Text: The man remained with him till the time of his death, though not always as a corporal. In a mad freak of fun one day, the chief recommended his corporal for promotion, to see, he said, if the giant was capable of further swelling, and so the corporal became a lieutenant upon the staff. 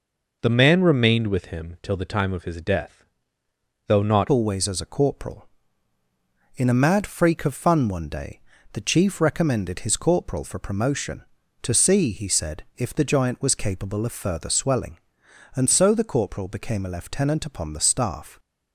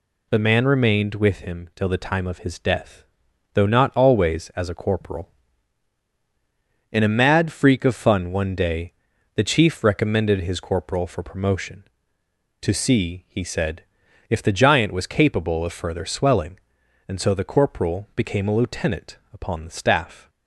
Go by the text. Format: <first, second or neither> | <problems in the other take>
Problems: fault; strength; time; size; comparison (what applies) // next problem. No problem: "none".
second | changes voice at "always"; from 4.3 s on; 14.0 s long